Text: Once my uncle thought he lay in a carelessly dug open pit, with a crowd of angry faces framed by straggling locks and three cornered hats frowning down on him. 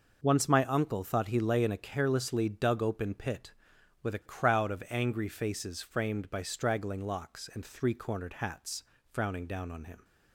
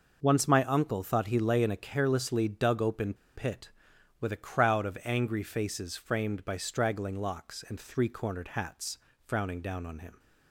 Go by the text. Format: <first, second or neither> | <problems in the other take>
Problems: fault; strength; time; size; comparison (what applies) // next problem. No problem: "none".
first | pauses between "open" and "pit"; slight; at 3.1 s; 0.20 s long // pauses between "hats" and "frowning"; slight; at 8.9 s; 0.30 s long; slight in the first